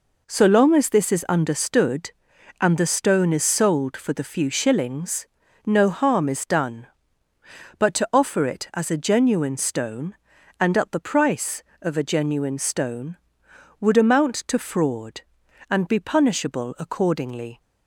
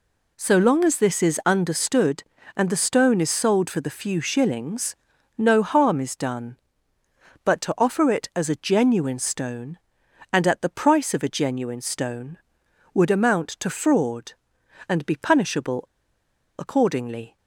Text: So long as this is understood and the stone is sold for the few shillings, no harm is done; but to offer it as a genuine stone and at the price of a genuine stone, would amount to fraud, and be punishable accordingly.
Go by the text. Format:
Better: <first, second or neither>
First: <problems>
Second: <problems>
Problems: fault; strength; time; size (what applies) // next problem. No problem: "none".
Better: first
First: none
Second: pauses between "punishable" and "accordingly"; noticeable; at 15.8 s; 0.75 s long